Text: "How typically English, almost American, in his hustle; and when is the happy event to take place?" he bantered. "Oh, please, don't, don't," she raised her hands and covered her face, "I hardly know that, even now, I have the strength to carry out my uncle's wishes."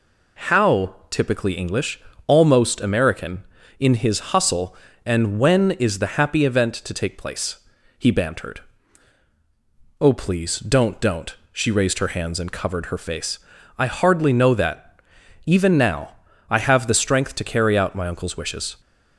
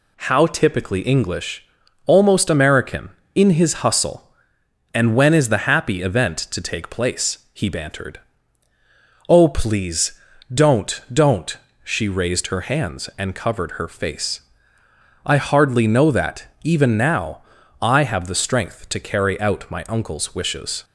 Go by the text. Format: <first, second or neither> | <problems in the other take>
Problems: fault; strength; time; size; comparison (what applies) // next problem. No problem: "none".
neither | none